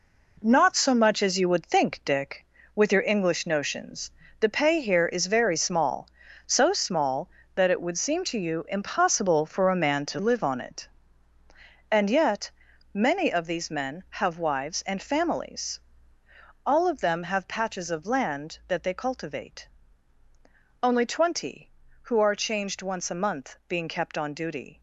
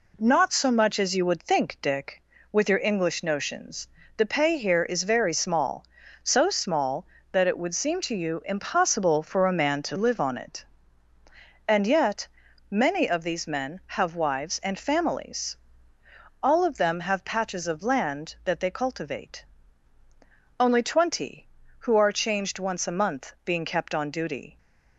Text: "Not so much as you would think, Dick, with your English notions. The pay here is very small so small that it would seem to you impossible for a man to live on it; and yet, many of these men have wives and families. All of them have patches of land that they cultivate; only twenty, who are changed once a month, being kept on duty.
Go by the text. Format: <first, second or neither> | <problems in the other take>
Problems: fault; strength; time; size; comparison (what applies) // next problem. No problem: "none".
second | gets quieter; strong; throughout; 8.5 dB